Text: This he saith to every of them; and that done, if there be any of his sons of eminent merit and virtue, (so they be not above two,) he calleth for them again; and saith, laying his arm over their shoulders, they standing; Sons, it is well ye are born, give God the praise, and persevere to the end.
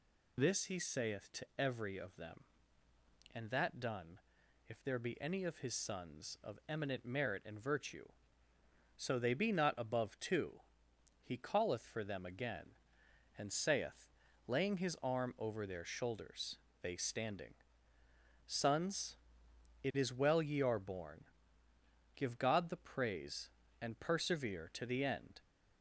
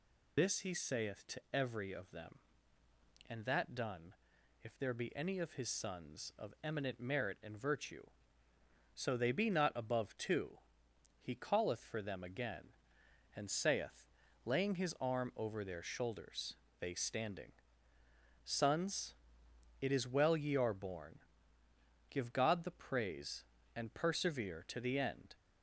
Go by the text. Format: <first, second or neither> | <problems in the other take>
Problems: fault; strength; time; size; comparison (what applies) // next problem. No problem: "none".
first | loses the start of "This"; at 0.3 s; 50 ms